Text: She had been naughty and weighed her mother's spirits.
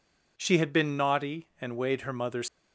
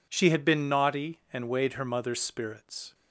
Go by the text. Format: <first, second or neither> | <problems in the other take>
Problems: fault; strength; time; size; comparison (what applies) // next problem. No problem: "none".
second | stops before "spirits"; at 2.4 s